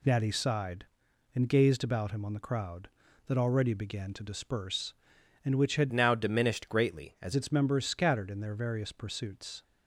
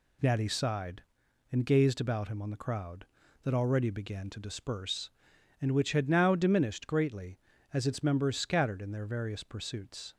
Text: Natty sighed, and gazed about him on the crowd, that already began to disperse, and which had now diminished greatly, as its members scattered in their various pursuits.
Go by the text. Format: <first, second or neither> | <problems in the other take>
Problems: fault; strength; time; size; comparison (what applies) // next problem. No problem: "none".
second | changes voice from "now" to "as"; from 5.9 to 7.3 s; 1.4 s long